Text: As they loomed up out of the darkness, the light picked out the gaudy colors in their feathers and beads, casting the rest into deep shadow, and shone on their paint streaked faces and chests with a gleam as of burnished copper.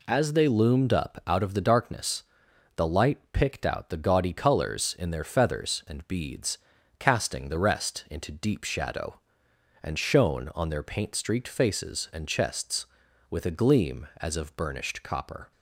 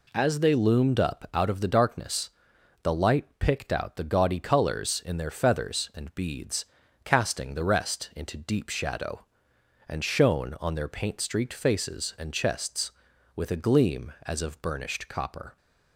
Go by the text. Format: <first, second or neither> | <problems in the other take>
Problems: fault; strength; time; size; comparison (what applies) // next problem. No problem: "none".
neither | none